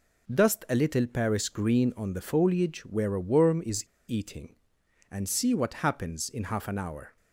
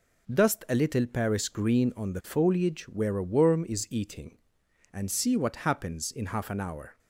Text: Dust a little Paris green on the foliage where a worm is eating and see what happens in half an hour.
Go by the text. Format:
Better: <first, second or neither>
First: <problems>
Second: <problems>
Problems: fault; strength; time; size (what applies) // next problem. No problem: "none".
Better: second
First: pauses between "is" and "eating"; slight; at 3.8 s; 0.24 s long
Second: none